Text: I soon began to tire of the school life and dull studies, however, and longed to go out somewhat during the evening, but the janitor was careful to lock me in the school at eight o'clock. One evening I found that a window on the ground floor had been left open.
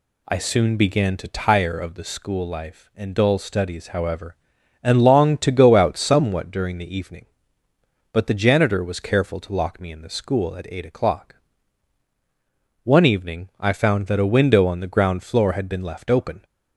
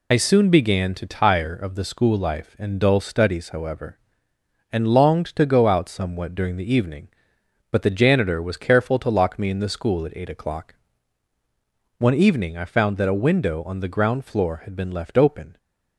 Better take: first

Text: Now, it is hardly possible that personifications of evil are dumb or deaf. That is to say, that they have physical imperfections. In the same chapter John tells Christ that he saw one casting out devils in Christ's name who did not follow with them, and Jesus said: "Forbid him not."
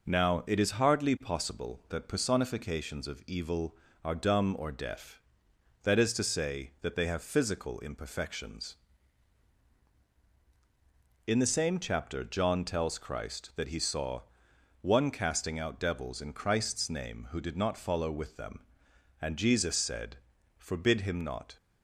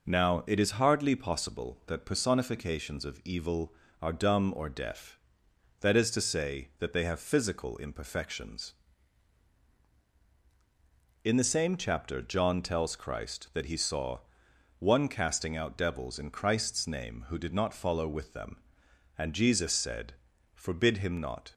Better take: neither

